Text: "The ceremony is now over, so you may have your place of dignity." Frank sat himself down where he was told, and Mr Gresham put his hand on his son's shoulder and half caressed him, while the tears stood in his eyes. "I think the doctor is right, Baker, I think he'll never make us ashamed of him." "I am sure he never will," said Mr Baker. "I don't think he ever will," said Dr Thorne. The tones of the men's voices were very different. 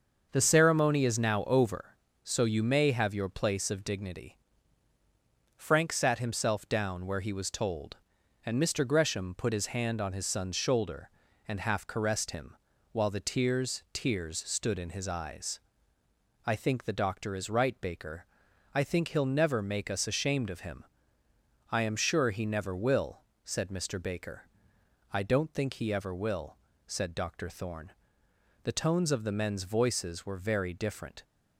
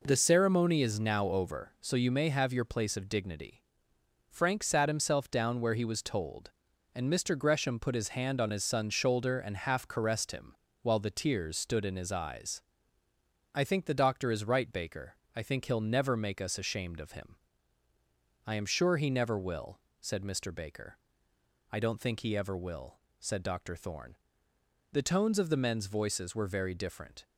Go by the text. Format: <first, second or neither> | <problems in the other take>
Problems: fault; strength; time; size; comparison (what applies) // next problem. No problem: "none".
second | starts louder than the rest; until 1.3 s; 6.5 dB // says "tears" twice; at 13.9 s